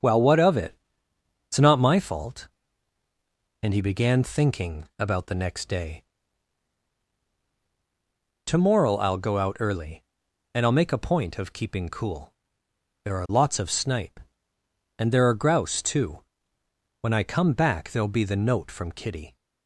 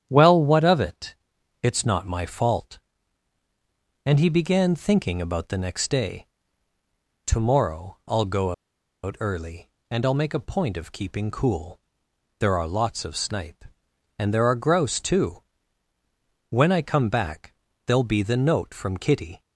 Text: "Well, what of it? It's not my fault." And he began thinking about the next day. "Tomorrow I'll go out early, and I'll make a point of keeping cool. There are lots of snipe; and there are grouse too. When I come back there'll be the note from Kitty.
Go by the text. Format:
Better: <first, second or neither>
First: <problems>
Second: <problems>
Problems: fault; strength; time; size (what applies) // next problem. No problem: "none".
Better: first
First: starts louder than the rest; until 1.7 s; 7 dB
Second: starts louder than the rest; strong; until 1.1 s; 9.5 dB // pauses between "go" and "out"; noticeable; at 8.5 s; 0.51 s long // pauses between "back" and "there'll"; slight; at 17.5 s; 0.32 s long